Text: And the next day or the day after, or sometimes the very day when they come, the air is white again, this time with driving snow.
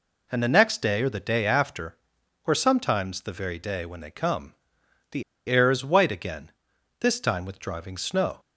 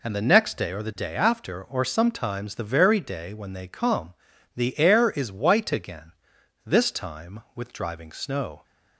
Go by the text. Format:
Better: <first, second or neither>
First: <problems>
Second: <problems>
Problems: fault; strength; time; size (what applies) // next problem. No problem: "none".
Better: second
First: pauses between "the" and "air"; slight; at 5.2 s; 0.24 s long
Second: none